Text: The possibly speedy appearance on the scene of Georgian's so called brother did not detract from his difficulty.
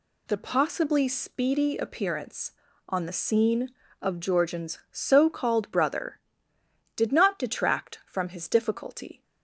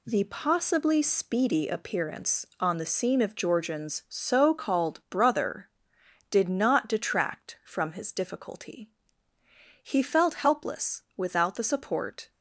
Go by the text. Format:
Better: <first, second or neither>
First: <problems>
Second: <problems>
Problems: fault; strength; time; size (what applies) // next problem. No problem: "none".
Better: first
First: none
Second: goes on to say "He felt helpless without the support"; strong; from 9.8 s on; 2.4 s long